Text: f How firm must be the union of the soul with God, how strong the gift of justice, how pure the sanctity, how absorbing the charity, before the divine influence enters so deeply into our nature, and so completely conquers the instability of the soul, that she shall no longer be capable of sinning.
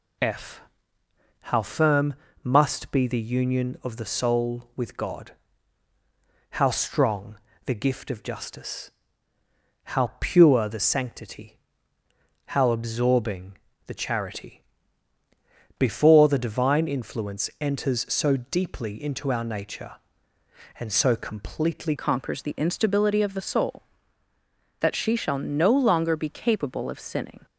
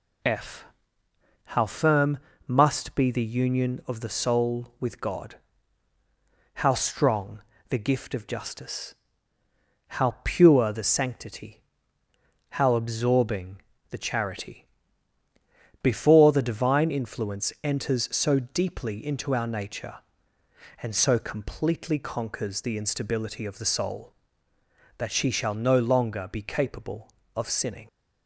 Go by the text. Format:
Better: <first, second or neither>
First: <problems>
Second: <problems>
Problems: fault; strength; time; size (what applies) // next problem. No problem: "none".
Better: second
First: pauses between "f" and "How"; noticeable; at 0.6 s; 0.80 s long // pauses between "firm" and "must"; slight; at 2.1 s; 0.28 s long // pauses between "strong" and "the"; slight; at 7.3 s; 0.28 s long // pauses between "absorbing" and "the"; slight; at 13.5 s; 0.28 s long // changes voice at "conquers"; from 21.9 s on; 5.5 s long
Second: pauses between "f" and "How"; noticeable; at 0.6 s; 0.80 s long // pauses between "firm" and "must"; slight; at 2.1 s; 0.28 s long // pauses between "strong" and "the"; slight; at 7.4 s; 0.28 s long // pauses between "absorbing" and "the"; slight; at 13.6 s; 0.28 s long